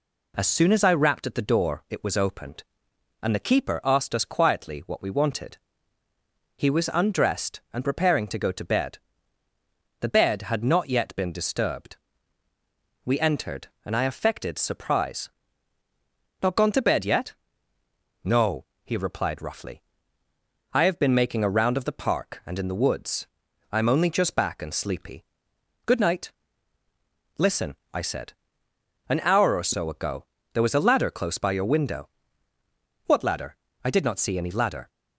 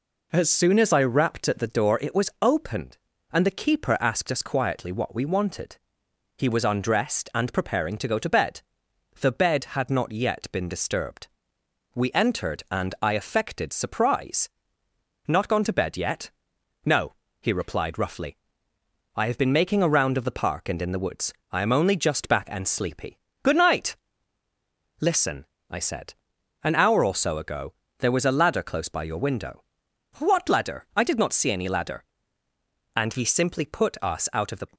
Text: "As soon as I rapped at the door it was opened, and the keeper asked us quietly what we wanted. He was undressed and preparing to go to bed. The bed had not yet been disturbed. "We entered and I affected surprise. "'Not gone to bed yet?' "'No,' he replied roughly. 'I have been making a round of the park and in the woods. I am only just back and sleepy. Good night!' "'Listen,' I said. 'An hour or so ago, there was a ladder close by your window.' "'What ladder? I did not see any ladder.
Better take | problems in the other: first | goes on to say "And he simply put us out of the"; strong; from 32.9 s on; 1.7 s long

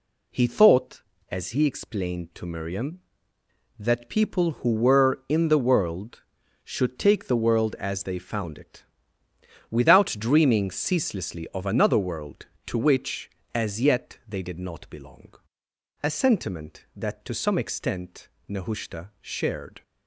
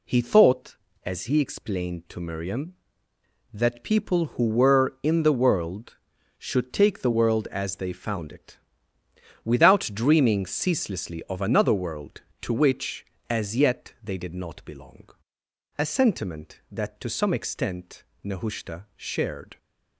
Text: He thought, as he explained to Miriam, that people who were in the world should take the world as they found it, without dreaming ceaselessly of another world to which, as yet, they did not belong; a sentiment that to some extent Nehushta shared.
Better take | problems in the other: neither | pauses between "extent" and "Nehushta"; slight; the same in both

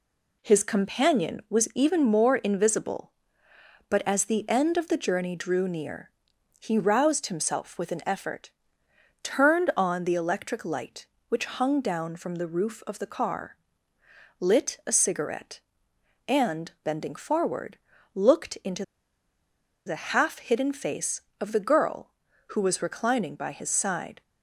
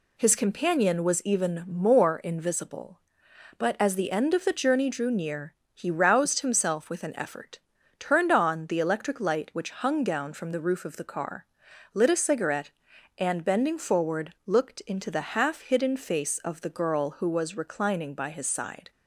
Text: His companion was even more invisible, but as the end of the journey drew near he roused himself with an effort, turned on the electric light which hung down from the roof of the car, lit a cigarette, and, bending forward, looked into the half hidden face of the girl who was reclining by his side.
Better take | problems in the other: second | pauses between "near" and "he"; noticeable; at 6.1 s; 0.50 s long; slight in the second // pauses between "into" and "the"; at 18.8 s; 1.0 s long

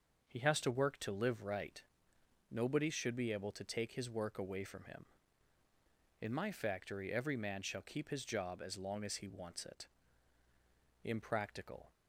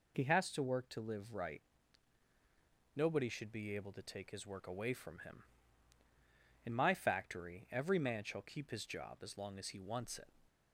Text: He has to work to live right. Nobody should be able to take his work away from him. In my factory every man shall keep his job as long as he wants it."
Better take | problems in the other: second | starts louder than the rest; until 1.2 s; 6.5 dB // goes on to say "Impractical"; noticeable; from 11.0 s on; 0.88 s long

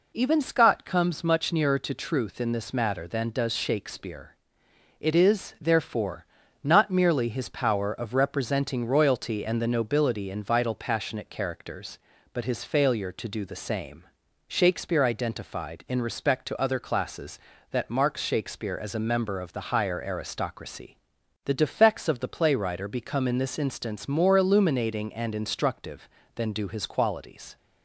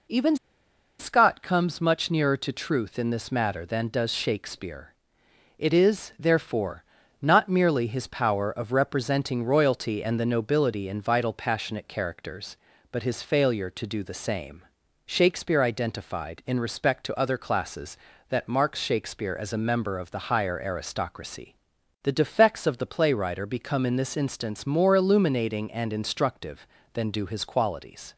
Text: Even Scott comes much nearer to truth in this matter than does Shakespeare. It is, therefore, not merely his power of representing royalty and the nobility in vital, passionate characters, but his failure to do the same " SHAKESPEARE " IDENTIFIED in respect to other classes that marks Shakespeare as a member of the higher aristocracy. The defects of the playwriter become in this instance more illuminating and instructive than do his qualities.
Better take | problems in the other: first | pauses between "Even" and "Scott"; noticeable; at 0.3 s; 0.64 s long

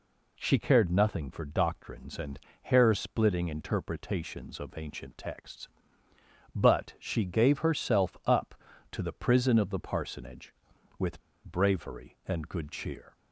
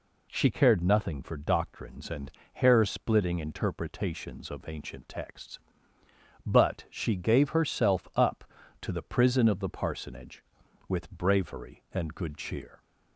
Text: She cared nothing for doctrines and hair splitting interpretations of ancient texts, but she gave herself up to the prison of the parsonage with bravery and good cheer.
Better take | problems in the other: second | pauses between "and" and "hair"; slight; at 2.3 s; 0.24 s long; slight in the second // pauses between "with" and "bravery"; slight; at 11.1 s; 0.24 s long

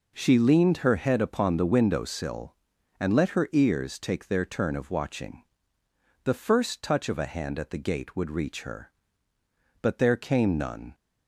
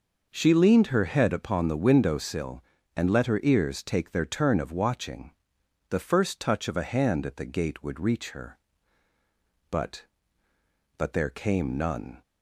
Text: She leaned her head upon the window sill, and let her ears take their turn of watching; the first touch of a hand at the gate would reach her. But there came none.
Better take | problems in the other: first | says "But" twice; at 10.9 s

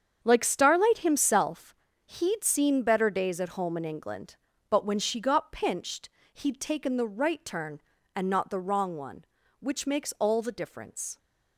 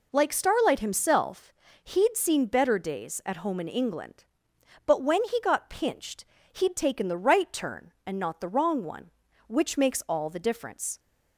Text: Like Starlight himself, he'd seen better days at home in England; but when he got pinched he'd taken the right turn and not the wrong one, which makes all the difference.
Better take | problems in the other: second | starts louder than the rest; strong; until 1.2 s; 7.5 dB // says "she" for "he"; at 4.9 s // pauses between "pinched" and "he'd"; slight; at 6.0 s; 0.24 s long; slight in the second

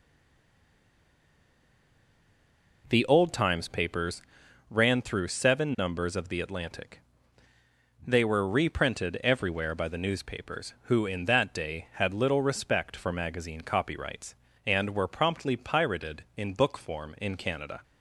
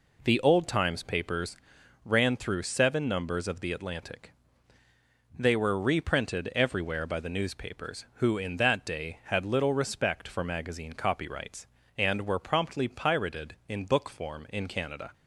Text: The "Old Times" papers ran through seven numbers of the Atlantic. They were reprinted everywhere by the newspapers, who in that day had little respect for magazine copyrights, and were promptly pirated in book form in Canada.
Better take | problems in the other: second | stays silent before the first word; strong; until 2.8 s; 2.8 s long // pauses between "papers" and "ran"; noticeable; at 4.2 s; 0.48 s long; noticeable in the second

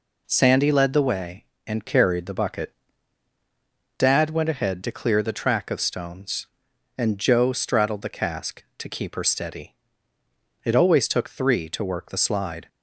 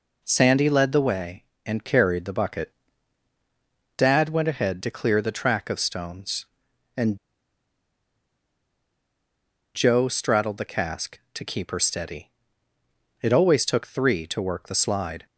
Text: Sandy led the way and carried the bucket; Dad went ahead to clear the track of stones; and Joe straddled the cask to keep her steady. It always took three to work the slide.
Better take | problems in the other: first | pauses between "and" and "Joe"; strong; at 7.1 s; 2.5 s long

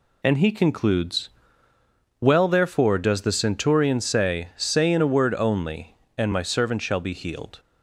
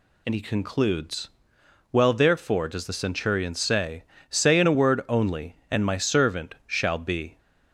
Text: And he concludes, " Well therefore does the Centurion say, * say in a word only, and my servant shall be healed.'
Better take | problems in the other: first | stops before "healed"; at 7.3 s

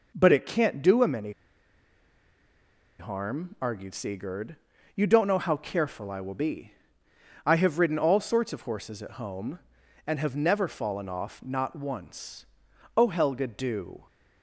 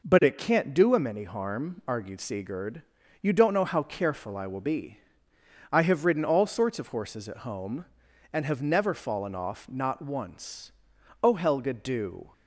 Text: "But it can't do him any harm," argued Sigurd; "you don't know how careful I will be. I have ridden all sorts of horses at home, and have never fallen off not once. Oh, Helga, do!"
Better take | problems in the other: second | pauses between "any" and "harm"; strong; at 1.3 s; 1.6 s long

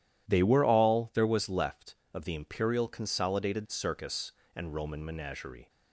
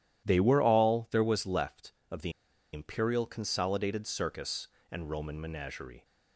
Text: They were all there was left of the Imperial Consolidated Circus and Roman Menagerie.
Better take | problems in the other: first | pauses between "the" and "Imperial"; at 2.3 s; 0.42 s long

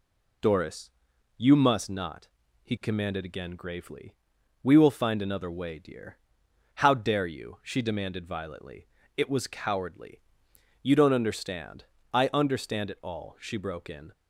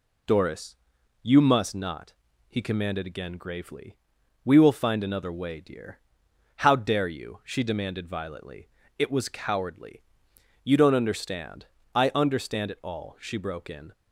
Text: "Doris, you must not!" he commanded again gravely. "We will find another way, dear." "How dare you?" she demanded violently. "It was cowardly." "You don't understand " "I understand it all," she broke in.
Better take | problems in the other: neither | none

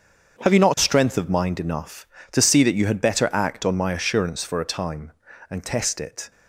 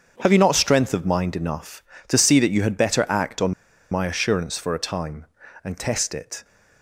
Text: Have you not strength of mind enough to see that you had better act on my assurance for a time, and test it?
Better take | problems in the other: first | starts louder than the rest; strong; until 1.2 s; 7 dB; strong in the first // pauses between "on" and "my"; at 3.5 s; 0.38 s long

